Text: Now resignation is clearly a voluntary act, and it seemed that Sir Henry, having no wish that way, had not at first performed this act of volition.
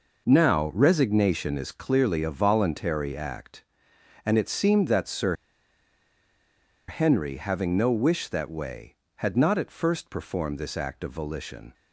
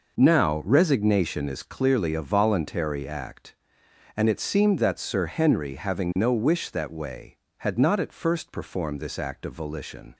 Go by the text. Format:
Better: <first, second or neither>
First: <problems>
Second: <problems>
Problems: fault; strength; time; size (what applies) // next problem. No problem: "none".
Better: second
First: pauses between "Sir" and "Henry"; strong; at 5.3 s; 1.5 s long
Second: none